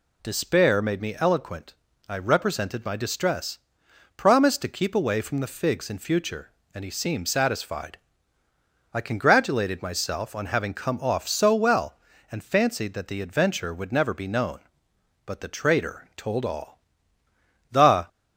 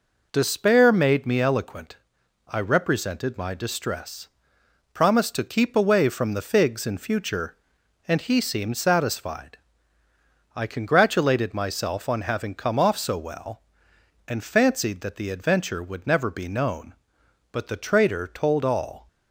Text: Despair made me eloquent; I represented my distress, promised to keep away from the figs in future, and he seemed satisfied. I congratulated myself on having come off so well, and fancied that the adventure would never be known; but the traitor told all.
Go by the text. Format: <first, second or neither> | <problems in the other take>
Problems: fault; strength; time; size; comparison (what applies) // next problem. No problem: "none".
second | goes on to say "The"; slight; from 17.6 s on; 0.38 s long